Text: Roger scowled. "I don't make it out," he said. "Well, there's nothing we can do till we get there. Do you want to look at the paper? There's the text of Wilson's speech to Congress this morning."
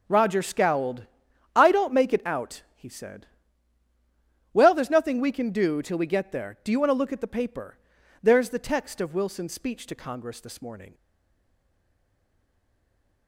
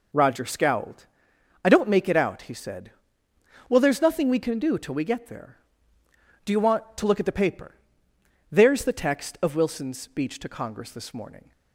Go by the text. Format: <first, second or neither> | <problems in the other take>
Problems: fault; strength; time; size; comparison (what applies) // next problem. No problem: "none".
second | stays silent after the last word; from 10.9 s on; 2.3 s long